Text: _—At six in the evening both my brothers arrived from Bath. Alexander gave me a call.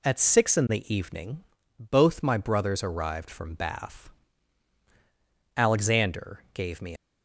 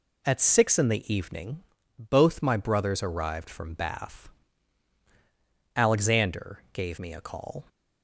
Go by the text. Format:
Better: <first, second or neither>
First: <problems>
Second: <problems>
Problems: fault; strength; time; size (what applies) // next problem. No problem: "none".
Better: second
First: pauses between "evening" and "both"; slight; at 1.4 s; 0.34 s long // stops before "a call"; at 6.9 s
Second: pauses between "evening" and "both"; slight; at 1.6 s; 0.34 s long